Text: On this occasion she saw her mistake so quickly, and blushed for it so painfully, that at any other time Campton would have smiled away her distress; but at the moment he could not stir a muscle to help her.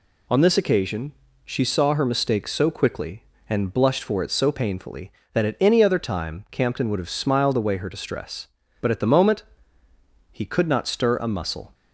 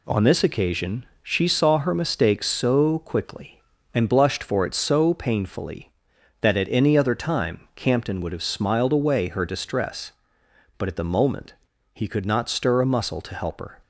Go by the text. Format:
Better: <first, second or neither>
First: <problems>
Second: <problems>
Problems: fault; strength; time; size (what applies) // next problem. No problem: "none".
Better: second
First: pauses between "occasion" and "she"; slight; at 1.1 s; 0.34 s long // pauses between "moment" and "he"; noticeable; at 9.4 s; 0.88 s long // stops before "to help her"; at 11.7 s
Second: pauses between "occasion" and "she"; slight; at 1.0 s; 0.16 s long // pauses between "moment" and "he"; at 11.5 s; 0.40 s long